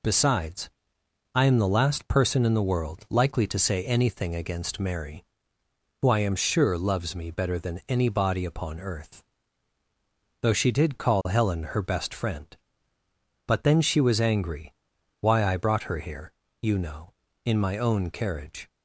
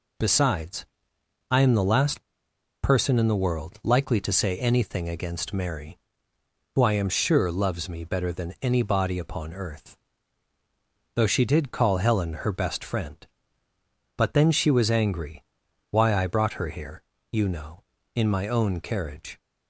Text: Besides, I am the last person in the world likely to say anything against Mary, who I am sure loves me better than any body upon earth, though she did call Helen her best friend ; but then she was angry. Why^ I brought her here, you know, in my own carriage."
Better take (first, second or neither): first